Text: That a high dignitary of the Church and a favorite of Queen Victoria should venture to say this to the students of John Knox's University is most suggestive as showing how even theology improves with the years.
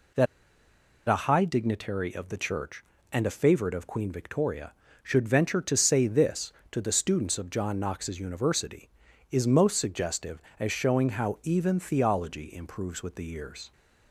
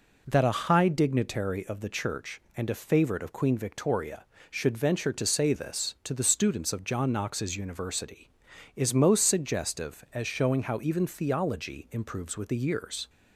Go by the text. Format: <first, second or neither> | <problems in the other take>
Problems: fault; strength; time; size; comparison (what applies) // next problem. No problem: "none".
second | pauses between "That" and "a"; noticeable; at 0.2 s; 0.81 s long